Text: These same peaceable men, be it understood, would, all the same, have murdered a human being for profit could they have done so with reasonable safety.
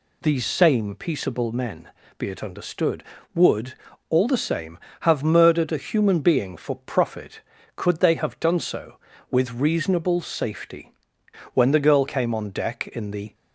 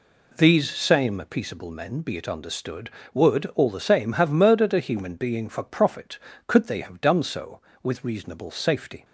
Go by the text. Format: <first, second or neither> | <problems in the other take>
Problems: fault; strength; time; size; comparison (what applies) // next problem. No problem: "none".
second | goes on to say "When the girl came on deck in the"; strong; from 11.5 s on; 1.8 s long